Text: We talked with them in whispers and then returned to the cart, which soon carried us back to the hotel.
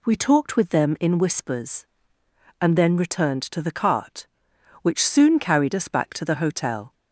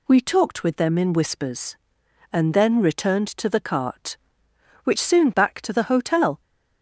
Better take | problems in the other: first | skips "carried us"; at 5.3 s

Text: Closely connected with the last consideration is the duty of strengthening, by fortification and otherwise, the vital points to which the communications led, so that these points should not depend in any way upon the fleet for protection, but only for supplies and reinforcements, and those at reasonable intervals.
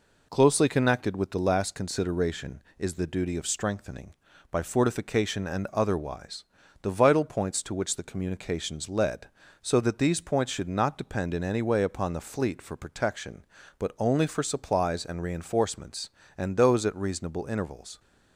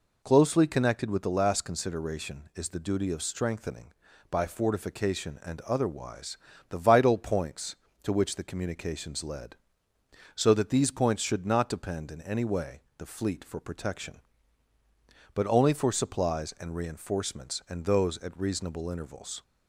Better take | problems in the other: first | skips "upon"; at 12.9 s

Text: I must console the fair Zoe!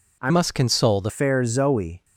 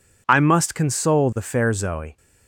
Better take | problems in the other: second | changes voice from "must" to "the"; from 0.2 to 1.1 s; 0.9 s long

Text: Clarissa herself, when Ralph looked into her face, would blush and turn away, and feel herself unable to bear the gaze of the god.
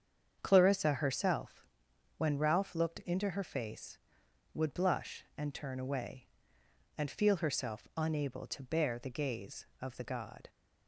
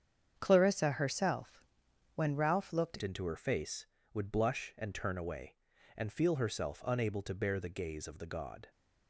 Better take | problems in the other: first | starts louder than the rest; strong; until 1.3 s; 8 dB; strong in the first // changes voice at "into"; from 3.0 s on; 5.6 s long

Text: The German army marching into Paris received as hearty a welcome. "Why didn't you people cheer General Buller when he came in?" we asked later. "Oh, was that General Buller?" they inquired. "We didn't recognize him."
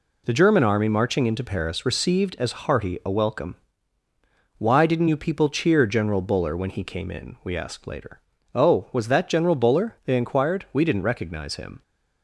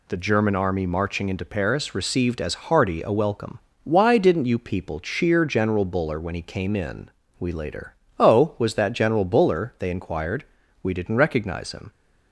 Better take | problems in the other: first | skips "asked"; at 7.5 s

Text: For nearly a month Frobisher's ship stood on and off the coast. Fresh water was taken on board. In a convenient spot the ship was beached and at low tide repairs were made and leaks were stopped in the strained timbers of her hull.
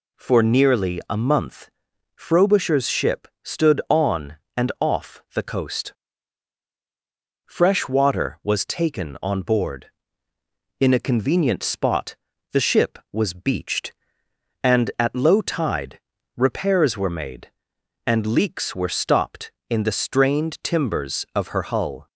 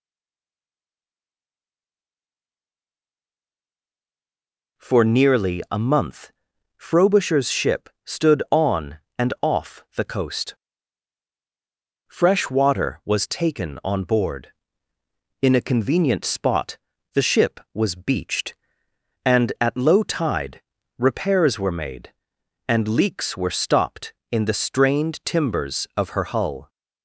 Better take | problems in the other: first | stays silent before the first word; strong; until 4.7 s; 4.7 s long // pauses between "month" and "Frobisher's"; noticeable; at 6.3 s; 0.46 s long; noticeable in the first // pauses between "ship" and "stood"; slight; at 7.8 s; 0.16 s long; slight in the first // pauses between "spot" and "the"; at 16.7 s; 0.38 s long; also in the first // pauses between "tide" and "repairs"; at 20.6 s; 0.38 s long; also in the first

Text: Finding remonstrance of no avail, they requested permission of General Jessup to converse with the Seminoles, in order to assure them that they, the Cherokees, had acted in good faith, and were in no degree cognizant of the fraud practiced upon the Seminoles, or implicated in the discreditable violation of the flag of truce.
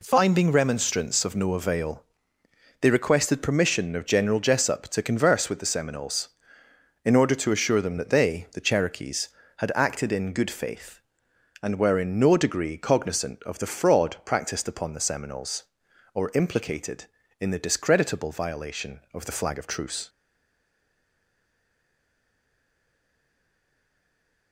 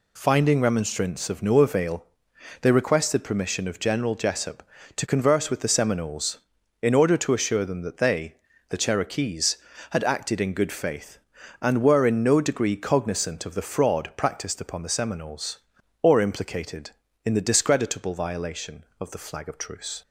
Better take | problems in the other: second | stays silent after the last word; strong; from 20.0 s on; 4.5 s long

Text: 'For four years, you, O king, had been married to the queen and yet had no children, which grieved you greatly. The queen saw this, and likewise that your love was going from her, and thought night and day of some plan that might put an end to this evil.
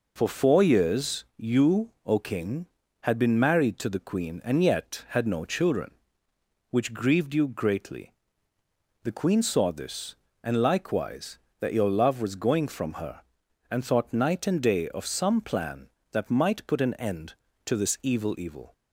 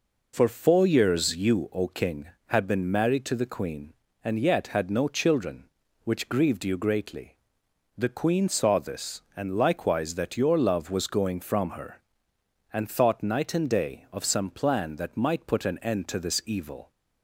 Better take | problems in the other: second | says "evil" twice; at 18.3 s

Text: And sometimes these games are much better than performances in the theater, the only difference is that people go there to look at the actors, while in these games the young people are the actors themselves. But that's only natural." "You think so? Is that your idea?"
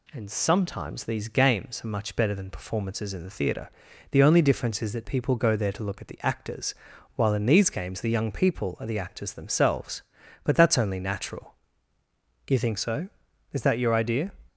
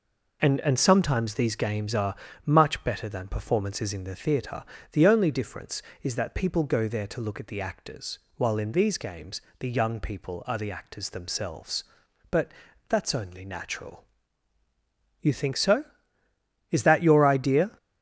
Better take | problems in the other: first | says "And" twice; at 0.6 s // pauses between "are" and "much"; slight; at 2.1 s; 0.30 s long // pauses between "games" and "the"; slight; at 9.4 s; 0.18 s long // pauses between "But" and "that's"; at 12.5 s; 0.38 s long

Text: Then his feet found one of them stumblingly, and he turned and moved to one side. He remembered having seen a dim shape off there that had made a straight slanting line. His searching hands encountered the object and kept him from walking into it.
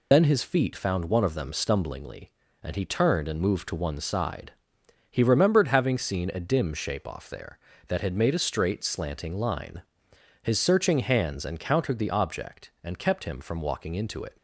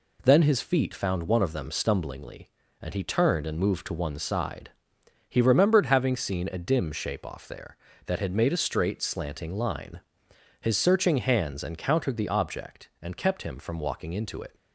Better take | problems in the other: second | loses the start of "Then"; at 0.1 s; 95 ms

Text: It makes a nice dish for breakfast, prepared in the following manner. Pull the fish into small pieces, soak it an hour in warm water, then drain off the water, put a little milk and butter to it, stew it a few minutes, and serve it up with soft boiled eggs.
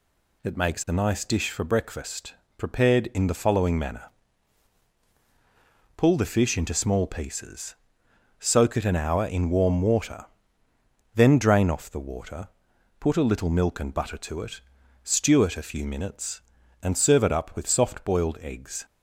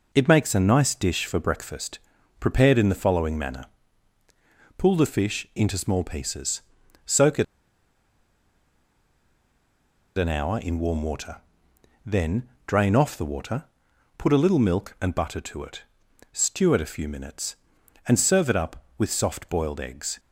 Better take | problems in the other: first | pauses between "it" and "an"; strong; at 7.4 s; 2.7 s long // pauses between "then" and "drain"; slight; at 12.4 s; 0.18 s long

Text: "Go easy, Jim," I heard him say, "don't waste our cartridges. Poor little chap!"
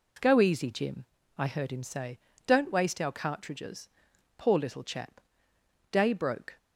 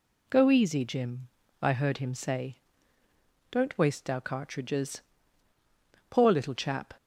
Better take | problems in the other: second | goes on to say "Day broke"; noticeable; from 5.9 s on; 0.66 s long

